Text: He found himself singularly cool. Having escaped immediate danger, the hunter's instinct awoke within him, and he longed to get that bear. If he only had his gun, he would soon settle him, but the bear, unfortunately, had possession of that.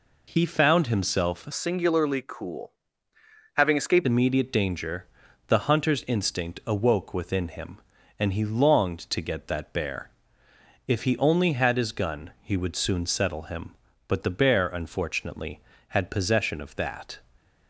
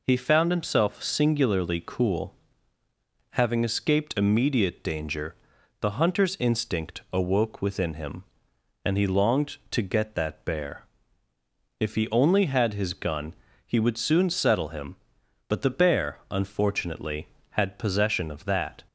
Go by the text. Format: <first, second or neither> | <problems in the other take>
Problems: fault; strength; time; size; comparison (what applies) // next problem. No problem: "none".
second | changes voice from "singularly" to "escaped"; from 1.5 to 4.0 s; 2.5 s long